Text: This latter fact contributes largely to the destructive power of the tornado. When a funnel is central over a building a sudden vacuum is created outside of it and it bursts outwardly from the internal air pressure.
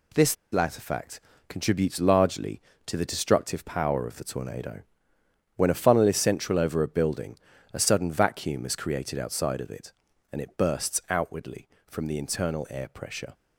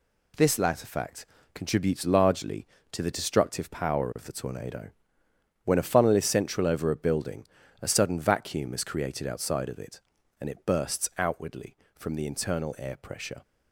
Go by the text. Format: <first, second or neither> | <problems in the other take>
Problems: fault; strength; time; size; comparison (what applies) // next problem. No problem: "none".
second | pauses between "This" and "latter"; slight; at 0.3 s; 0.18 s long // pauses between "fact" and "contributes"; slight; at 1.1 s; 0.28 s long; slight in the second // pauses between "building" and "a"; slight; at 7.3 s; 0.34 s long; slight in the second